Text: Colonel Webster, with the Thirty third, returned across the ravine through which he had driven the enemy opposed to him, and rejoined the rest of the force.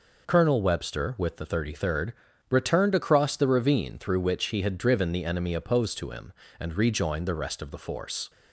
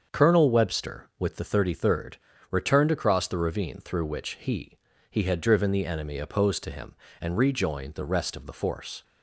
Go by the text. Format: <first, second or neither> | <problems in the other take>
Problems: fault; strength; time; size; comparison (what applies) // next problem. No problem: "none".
first | starts louder than the rest; until 1.2 s; 7 dB // says "he" twice; at 5.1 s